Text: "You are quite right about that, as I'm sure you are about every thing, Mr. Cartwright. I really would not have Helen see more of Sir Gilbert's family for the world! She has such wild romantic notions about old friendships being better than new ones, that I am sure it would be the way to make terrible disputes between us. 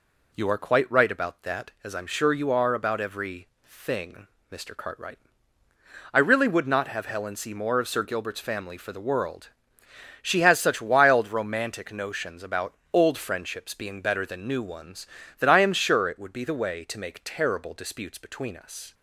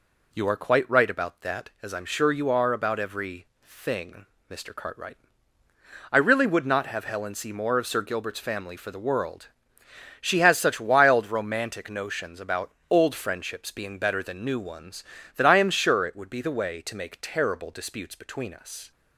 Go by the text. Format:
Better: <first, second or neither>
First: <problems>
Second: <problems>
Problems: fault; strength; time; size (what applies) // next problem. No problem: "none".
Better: neither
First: pauses between "every" and "thing"; slight; at 3.4 s; 0.18 s long // pauses between "about" and "old"; slight; at 12.7 s; 0.20 s long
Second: pauses between "every" and "thing"; slight; at 3.4 s; 0.18 s long // pauses between "about" and "old"; slight; at 12.7 s; 0.20 s long